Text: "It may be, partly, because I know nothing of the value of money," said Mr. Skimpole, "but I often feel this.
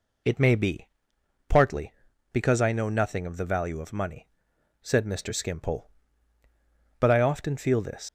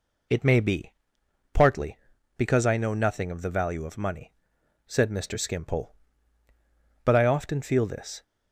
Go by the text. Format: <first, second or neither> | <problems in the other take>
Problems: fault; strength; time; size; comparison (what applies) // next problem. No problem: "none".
second | leaves "this" unfinished; at 8.0 s; 90 ms